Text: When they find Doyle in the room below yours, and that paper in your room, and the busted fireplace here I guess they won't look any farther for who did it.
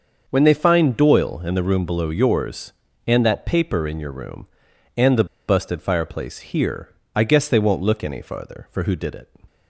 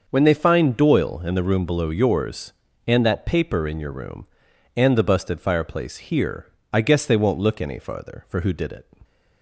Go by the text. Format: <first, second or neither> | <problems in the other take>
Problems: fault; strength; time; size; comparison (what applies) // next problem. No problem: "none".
second | starts louder than the rest; until 1.2 s; 6.5 dB; also in the second // pauses between "the" and "busted"; slight; at 5.2 s; 0.23 s long // pauses between "here" and "I"; slight; at 6.9 s; 0.22 s long; slight in the second